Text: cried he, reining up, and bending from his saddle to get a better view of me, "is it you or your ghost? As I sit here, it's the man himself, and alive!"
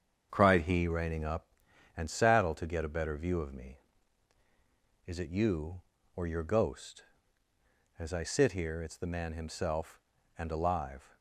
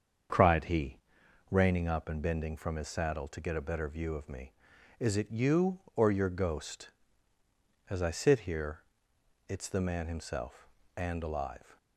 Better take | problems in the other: second | starts louder than the rest; strong; until 1.3 s; 7.5 dB; also in the second // skips "bending from his"; at 2.0 s

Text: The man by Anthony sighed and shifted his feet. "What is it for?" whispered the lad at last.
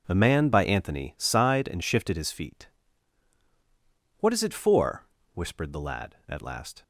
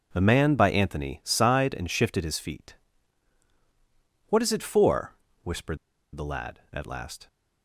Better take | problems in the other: first | pauses between "whispered" and "the"; at 5.7 s; 0.37 s long

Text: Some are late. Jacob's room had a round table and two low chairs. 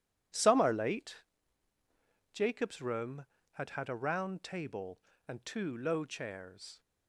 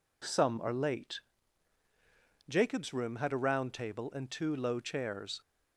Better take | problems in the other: second | says "had" twice; at 3.6 s

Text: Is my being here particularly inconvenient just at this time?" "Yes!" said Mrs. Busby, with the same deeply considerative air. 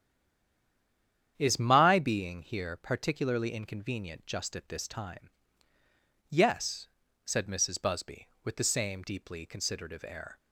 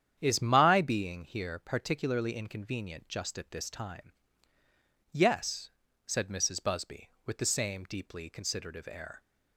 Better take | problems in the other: second | stays silent before the first word; noticeable; until 1.3 s; 1.3 s long // starts louder than the rest; strong; until 2.3 s; 9 dB; strong in the second

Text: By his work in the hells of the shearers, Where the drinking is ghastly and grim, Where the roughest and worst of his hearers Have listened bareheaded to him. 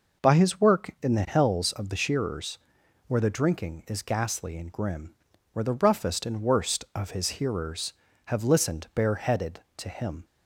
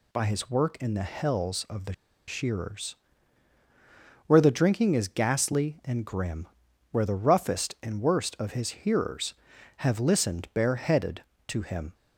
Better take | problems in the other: first | pauses between "the" and "shearers"; slight; at 1.9 s; 0.34 s long

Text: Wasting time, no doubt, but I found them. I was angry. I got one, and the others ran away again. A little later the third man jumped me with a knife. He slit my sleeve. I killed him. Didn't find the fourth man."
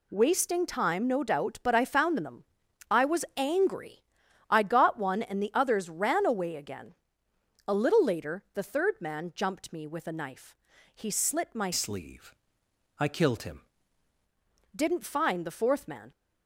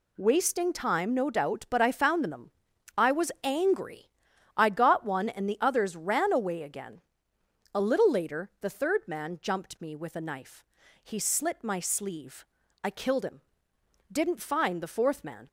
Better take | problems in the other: second | changes voice from "sleeve" to "him"; from 11.7 to 13.6 s; 1.9 s long

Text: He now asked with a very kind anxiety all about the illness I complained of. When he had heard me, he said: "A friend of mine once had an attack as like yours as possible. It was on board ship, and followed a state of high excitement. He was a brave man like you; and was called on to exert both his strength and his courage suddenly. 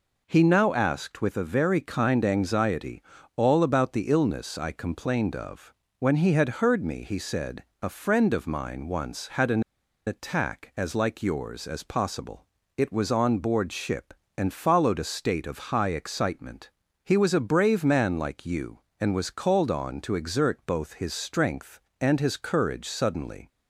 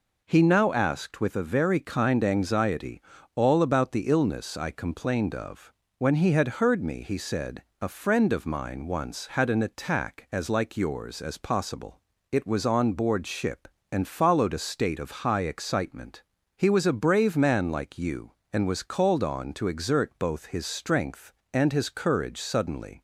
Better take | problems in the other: second | pauses between "anxiety" and "all"; slight; at 3.0 s; 0.34 s long; slight in the second // pauses between "an" and "attack"; at 9.6 s; 0.44 s long

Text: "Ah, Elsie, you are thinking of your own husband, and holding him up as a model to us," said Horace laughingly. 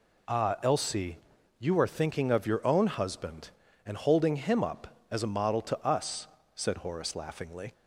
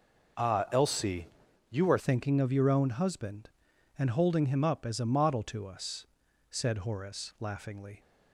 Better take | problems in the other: first | changes voice at "thinking"; from 1.9 s on; 6.1 s long

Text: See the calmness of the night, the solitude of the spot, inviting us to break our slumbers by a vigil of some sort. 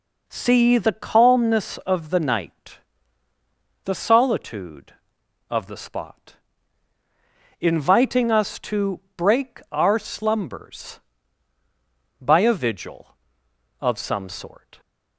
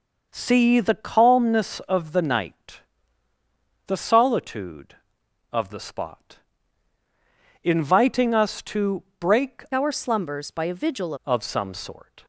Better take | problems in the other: first | pauses between "to" and "break"; slight; at 9.0 s; 0.16 s long; slight in the first // changes voice from "our" to "vigil"; from 9.7 to 11.1 s; 1.4 s long

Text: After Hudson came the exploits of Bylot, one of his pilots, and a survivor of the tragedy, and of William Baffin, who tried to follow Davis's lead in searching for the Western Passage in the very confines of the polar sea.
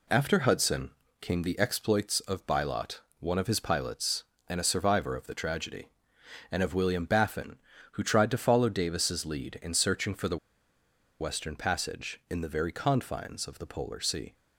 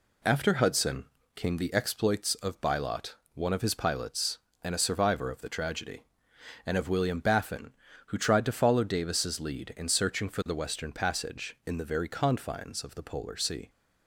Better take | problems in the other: second | pauses between "Hudson" and "came"; slight; at 0.9 s; 0.28 s long; slight in the second // pauses between "the" and "Western"; noticeable; at 10.3 s; 0.82 s long

